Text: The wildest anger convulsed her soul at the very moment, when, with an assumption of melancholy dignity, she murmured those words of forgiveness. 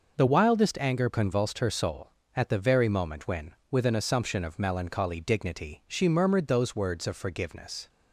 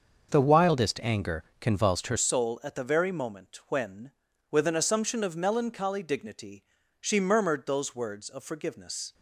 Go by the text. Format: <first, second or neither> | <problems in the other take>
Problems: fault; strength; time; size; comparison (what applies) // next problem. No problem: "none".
first | starts louder than the rest; until 1.3 s; 6.5 dB // pauses between "anger" and "convulsed"; slight; at 1.4 s; 0.18 s long // changes voice at "soul"; from 2.1 s on; 7.0 s long